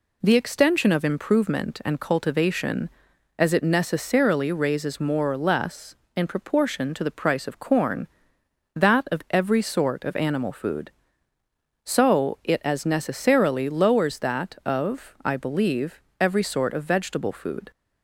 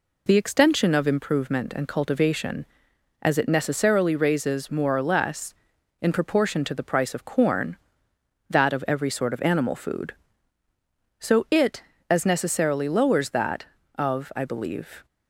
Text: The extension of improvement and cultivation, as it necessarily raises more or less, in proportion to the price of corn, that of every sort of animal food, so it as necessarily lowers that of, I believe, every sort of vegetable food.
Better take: first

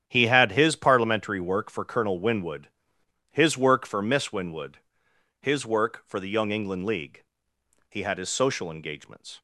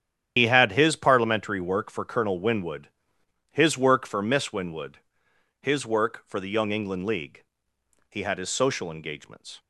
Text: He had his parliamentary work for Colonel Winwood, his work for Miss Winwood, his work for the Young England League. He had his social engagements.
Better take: first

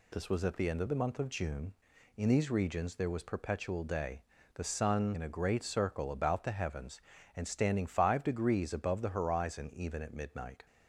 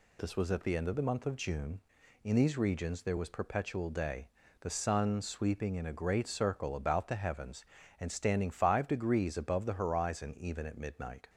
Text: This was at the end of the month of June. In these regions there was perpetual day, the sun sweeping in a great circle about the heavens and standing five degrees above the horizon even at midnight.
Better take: second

